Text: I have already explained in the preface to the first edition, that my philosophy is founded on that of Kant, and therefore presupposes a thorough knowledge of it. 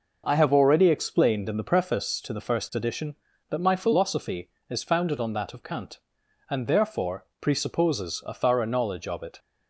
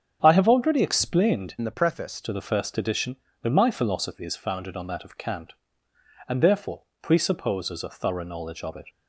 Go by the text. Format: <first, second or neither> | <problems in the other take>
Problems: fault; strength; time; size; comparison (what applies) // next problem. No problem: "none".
first | starts louder than the rest; strong; until 1.2 s; 7.5 dB // changes voice from "in" to "preface"; from 1.5 to 2.2 s; 0.7 s long // pauses between "therefore" and "presupposes"; slight; at 6.8 s; 0.20 s long